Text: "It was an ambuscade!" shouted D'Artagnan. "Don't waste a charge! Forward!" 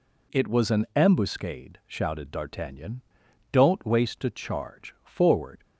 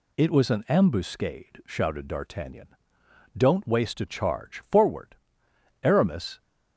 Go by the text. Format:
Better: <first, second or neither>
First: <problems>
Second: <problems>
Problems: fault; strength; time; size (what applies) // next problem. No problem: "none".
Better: first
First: none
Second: goes on to say "Aramis"; from 5.8 s on; 0.58 s long